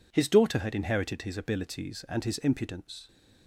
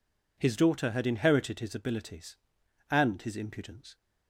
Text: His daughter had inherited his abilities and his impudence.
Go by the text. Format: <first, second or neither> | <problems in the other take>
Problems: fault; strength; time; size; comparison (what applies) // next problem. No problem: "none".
neither | none